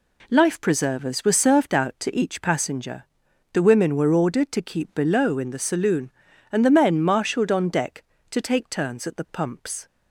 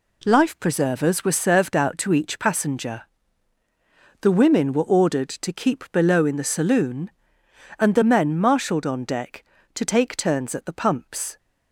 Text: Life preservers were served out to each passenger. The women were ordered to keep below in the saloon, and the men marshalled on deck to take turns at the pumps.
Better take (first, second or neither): neither